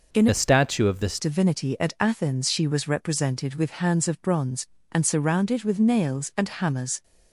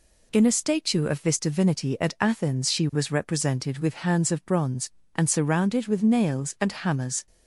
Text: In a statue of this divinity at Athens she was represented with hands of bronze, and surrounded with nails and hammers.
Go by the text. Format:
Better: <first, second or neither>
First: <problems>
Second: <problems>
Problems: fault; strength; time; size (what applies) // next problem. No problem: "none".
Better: second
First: changes voice from "a" to "this"; from 0.2 to 1.1 s; 0.9 s long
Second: none